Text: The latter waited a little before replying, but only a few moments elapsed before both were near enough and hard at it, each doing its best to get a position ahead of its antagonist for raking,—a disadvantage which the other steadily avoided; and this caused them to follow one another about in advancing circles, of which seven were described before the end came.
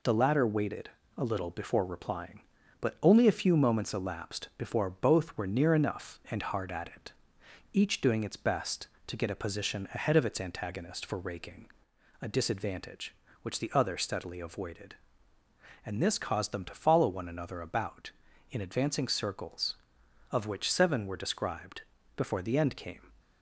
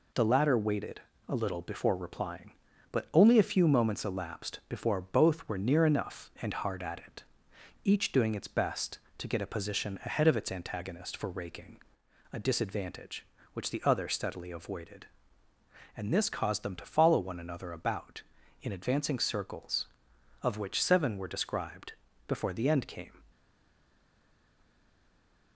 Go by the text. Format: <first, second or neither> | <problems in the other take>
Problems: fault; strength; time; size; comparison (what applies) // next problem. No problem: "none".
first | pauses between "waited" and "a"; slight; at 1.0 s; 0.28 s long; slight in the first // pauses between "described" and "before"; slight; at 21.9 s; 0.34 s long; slight in the first // stays silent after the last word; from 23.3 s on; 2.2 s long